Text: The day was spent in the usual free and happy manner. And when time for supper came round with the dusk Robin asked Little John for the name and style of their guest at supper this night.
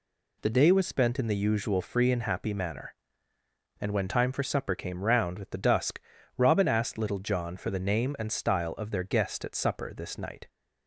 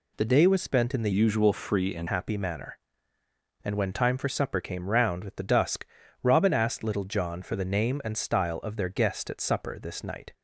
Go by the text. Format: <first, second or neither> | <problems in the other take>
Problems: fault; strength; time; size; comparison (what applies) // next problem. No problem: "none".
first | changes voice from "usual" to "and"; from 1.1 to 2.0 s; 0.9 s long // pauses between "dusk" and "Robin"; at 5.8 s; 0.38 s long; also in the first